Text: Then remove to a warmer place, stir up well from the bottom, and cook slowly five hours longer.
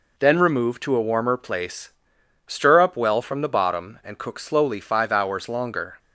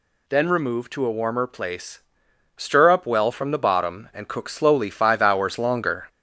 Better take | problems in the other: first | gets louder; throughout; 3.5 dB

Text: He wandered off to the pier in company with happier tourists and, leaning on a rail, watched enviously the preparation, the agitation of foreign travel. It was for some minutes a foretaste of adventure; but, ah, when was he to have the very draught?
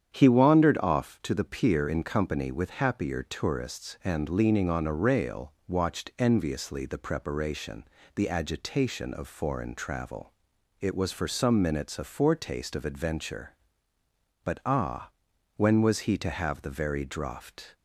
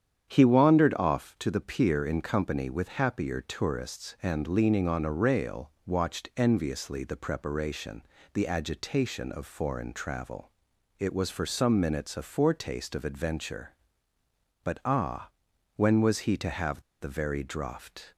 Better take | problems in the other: first | starts louder than the rest; strong; until 1.3 s; 9 dB; strong in the first // pauses between "have" and "the"; slight; at 16.8 s; 0.19 s long

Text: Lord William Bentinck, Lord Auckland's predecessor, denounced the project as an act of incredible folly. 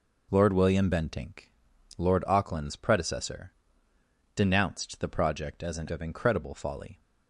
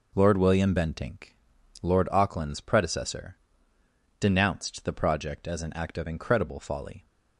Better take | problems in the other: second | skips "act"; at 5.8 s

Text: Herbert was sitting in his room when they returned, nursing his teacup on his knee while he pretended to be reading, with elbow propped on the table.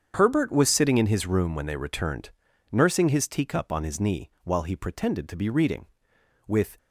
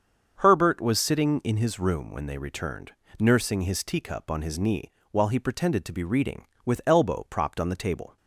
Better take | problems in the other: second | starts louder than the rest; strong; until 1.1 s; 7.5 dB; also in the second // pauses between "knee" and "while"; slight; at 4.2 s; 0.16 s long; slight in the second // stops before "elbow propped on the table"; at 6.7 s

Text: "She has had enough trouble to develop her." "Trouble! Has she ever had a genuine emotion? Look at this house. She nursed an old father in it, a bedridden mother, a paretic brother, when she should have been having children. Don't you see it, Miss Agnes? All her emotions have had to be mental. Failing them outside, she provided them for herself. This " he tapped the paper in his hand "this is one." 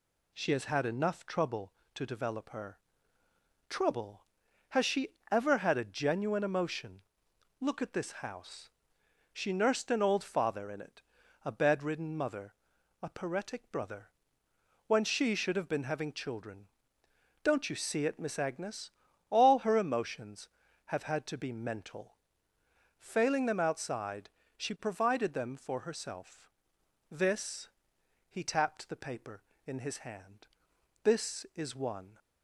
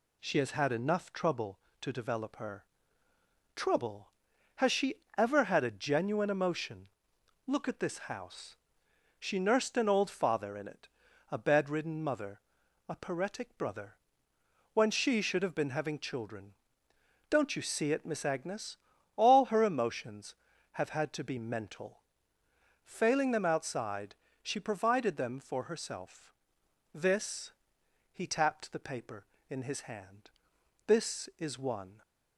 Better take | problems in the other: neither | pauses between "she" and "ever"; slight; the same in both // pauses between "hand" and "this"; noticeable; the same in both

